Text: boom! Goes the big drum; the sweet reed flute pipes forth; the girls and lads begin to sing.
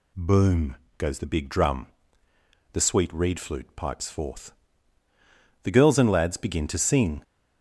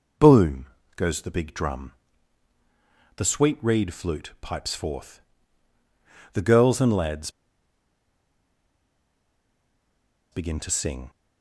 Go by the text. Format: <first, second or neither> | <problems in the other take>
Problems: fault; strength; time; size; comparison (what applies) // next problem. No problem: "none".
first | pauses between "lads" and "begin"; strong; at 7.2 s; 3.0 s long